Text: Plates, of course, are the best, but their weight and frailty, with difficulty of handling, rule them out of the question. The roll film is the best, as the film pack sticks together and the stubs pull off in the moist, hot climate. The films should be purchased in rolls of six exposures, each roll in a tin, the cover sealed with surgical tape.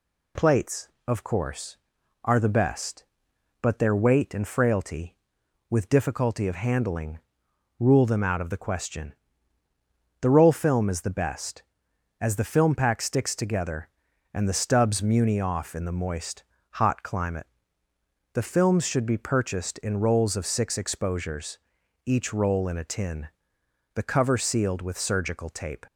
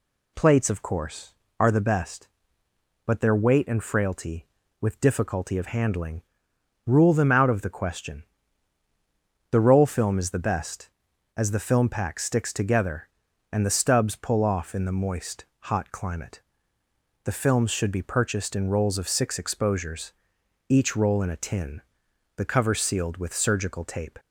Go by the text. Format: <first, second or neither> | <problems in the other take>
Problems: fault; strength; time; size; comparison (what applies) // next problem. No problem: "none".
second | says "muni" for "pull"; at 15.0 s